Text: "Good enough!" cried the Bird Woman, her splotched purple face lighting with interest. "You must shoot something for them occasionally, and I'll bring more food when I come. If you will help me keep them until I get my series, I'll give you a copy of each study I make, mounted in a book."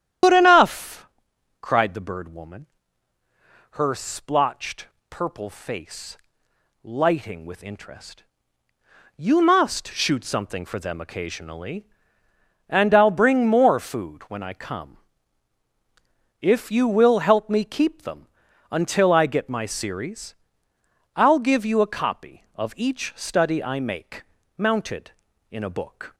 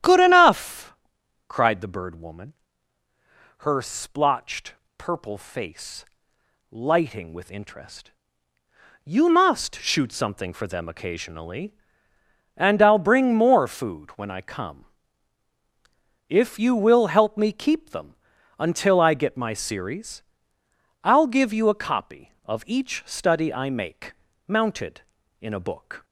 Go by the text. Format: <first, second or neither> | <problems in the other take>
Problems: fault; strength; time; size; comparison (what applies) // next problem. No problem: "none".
second | loses the start of "Good"; at 0.2 s; 80 ms // starts louder than the rest; strong; until 1.7 s; 10 dB; strong in the second // pauses between "splotched" and "purple"; slight; at 4.8 s; 0.23 s long; slight in the second // pauses between "face" and "lighting"; noticeable; at 6.1 s; 0.64 s long; noticeable in the second // pauses between "them" and "until"; at 18.2 s; 0.44 s long; also in the second